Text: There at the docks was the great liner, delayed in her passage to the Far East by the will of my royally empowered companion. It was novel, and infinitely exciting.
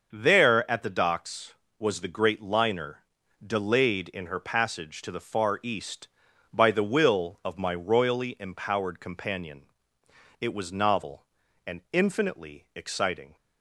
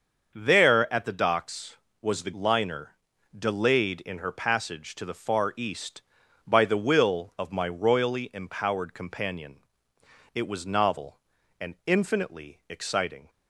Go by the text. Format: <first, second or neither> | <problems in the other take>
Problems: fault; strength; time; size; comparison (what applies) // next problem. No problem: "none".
first | starts louder than the rest; until 1.3 s; 6.5 dB; also in the first // skips "great"; at 2.3 s